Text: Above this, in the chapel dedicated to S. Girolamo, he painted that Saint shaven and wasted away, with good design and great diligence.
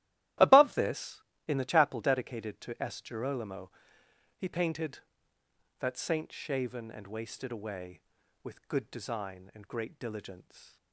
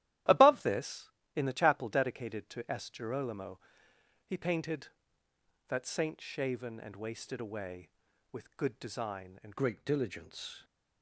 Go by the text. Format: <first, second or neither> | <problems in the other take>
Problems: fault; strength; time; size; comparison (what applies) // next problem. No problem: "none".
first | starts louder than the rest; strong; until 1.5 s; 13.5 dB; strong in the first // changes voice at "great"; from 9.5 s on; 1.1 s long